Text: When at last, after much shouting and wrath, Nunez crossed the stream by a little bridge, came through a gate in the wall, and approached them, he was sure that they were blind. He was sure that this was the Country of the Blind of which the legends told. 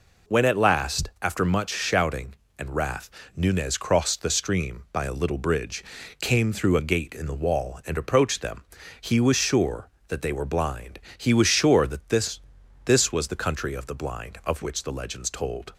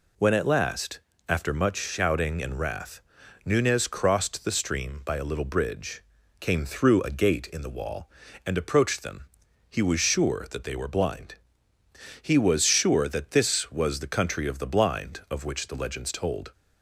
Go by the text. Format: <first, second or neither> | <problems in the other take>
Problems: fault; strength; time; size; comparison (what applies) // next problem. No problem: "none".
second | says "this" twice; at 12.8 s